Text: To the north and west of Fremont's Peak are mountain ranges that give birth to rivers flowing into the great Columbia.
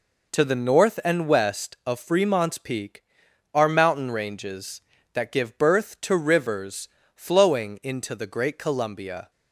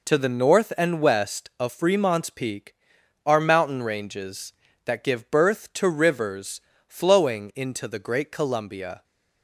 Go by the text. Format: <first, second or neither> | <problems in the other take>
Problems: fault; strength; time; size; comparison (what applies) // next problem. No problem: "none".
neither | pauses between "rivers" and "flowing"; slight; the same in both